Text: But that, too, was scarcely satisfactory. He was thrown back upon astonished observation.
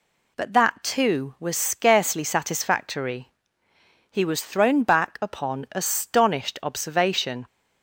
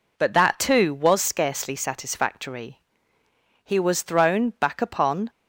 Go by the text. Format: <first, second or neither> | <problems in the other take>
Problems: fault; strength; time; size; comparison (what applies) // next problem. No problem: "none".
first | stops before "astonished observation"; at 5.2 s